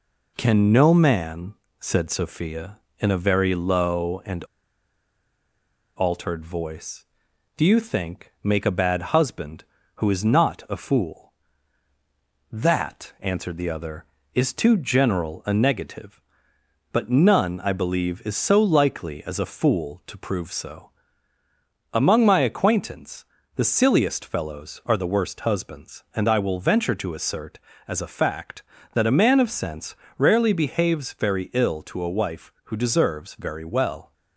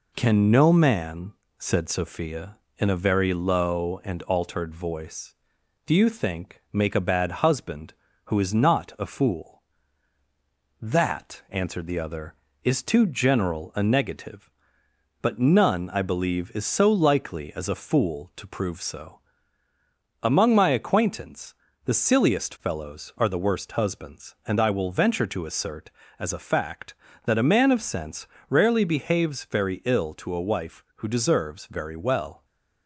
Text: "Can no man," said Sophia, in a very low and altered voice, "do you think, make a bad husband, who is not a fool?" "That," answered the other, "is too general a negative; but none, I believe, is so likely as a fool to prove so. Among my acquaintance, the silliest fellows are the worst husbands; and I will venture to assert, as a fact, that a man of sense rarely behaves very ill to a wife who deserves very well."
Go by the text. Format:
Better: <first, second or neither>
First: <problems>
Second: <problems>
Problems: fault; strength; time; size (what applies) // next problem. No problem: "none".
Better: second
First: pauses between "and" and "altered"; strong; at 4.4 s; 1.5 s long // pauses between "sense" and "rarely"; slight; at 29.9 s; 0.24 s long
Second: pauses between "sense" and "rarely"; slight; at 28.2 s; 0.24 s long